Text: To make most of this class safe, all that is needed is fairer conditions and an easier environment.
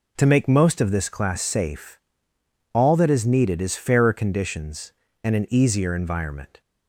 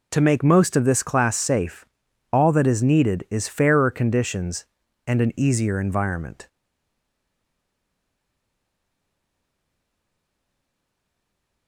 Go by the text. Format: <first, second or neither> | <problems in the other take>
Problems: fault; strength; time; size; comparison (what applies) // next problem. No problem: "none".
first | stays silent after the last word; strong; from 6.4 s on; 5.2 s long